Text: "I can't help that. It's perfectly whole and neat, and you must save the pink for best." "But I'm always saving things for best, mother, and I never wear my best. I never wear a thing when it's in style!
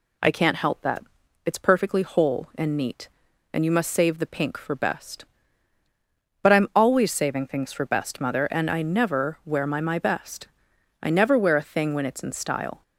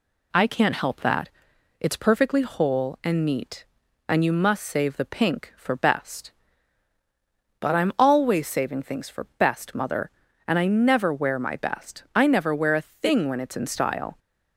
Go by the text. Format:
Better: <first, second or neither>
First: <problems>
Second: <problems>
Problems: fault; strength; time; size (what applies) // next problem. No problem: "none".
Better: second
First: says "my" twice; at 9.7 s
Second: none